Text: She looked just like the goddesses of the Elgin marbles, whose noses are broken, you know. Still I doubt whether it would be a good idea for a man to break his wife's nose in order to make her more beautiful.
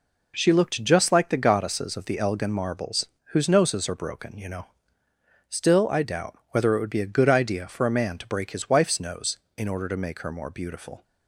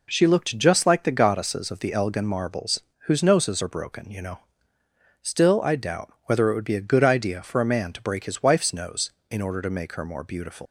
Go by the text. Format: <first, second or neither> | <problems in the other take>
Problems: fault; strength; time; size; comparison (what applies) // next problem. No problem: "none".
first | leaves "beautiful" unfinished; at 10.6 s; 110 ms